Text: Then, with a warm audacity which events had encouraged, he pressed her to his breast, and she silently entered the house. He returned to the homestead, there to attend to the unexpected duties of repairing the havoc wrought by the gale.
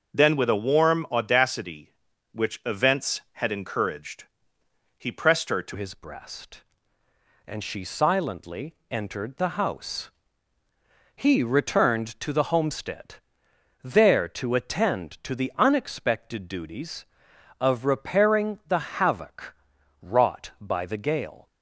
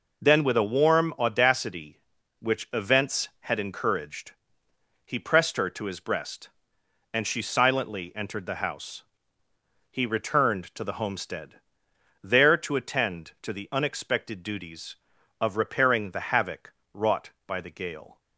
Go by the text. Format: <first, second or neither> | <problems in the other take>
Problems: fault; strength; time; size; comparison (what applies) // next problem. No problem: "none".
second | starts louder than the rest; until 1.2 s; 6 dB // changes voice at "his"; from 5.7 s on; 15.7 s long // pauses between "silently" and "entered"; slight; at 8.7 s; 0.16 s long // pauses between "havoc" and "wrought"; noticeable; at 19.5 s; 0.48 s long; slight in the second